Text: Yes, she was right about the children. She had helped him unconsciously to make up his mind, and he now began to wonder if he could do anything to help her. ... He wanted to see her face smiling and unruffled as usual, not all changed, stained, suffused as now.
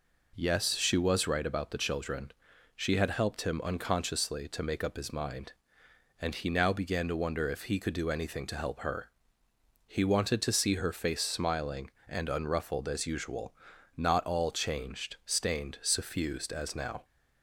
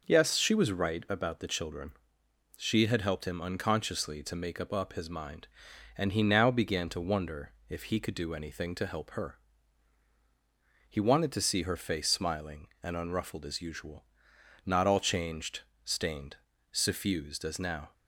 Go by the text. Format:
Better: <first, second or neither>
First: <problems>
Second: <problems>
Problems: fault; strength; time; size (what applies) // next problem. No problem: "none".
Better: first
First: none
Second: says "up" twice; at 4.7 s // pauses between "wonder" and "if"; slight; at 7.5 s; 0.16 s long